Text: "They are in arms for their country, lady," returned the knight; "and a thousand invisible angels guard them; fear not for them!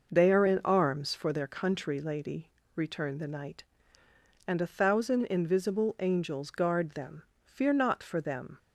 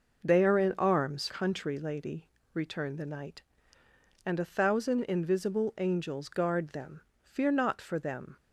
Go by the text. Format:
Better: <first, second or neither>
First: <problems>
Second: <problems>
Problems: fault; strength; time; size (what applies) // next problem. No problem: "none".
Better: first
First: none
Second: skips "for their"; at 1.2 s